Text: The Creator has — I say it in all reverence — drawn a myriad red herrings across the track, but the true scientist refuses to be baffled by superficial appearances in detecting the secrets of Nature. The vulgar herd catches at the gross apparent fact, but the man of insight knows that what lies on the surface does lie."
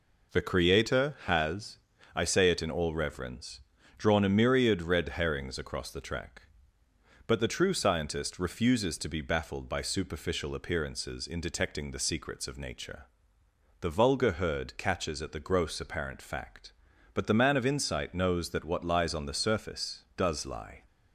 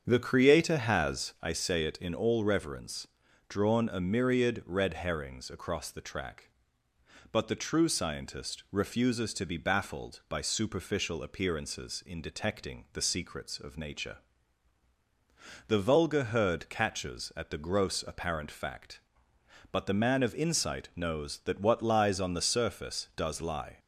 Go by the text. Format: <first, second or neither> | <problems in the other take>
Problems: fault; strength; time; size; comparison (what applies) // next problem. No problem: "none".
first | starts louder than the rest; strong; until 1.6 s; 7.5 dB